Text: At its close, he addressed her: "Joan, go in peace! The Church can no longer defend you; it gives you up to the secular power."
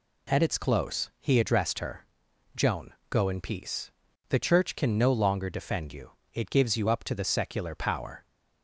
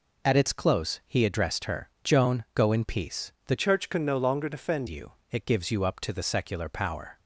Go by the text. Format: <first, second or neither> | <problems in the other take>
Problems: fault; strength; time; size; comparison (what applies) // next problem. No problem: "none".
first | changes voice from "Church" to "defend"; from 3.5 to 4.8 s; 1.3 s long